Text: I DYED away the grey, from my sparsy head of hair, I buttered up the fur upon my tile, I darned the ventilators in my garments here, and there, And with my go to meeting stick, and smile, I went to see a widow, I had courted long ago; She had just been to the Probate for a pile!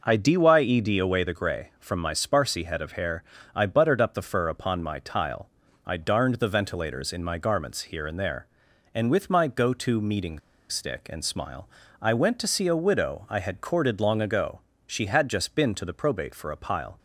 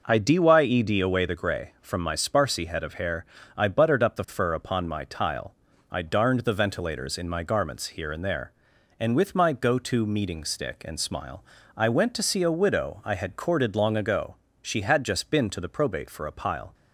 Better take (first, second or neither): second